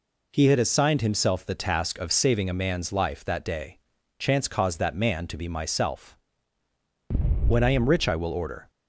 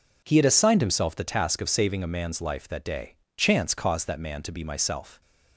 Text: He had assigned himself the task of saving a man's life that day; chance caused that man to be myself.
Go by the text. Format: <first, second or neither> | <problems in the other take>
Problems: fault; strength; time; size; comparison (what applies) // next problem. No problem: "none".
second | goes on to say "When I am rich I will order"; noticeable; from 7.4 s on; 1.2 s long